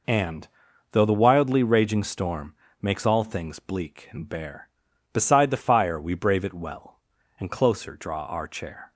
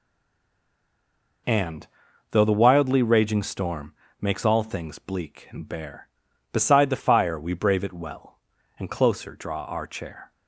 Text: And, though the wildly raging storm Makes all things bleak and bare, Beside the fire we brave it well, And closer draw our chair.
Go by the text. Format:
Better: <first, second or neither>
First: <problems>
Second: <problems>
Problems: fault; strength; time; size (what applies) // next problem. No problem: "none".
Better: first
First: pauses between "storm" and "Makes"; slight; at 2.5 s; 0.30 s long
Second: stays silent before the first word; noticeable; until 1.4 s; 1.4 s long // pauses between "storm" and "Makes"; slight; at 3.9 s; 0.30 s long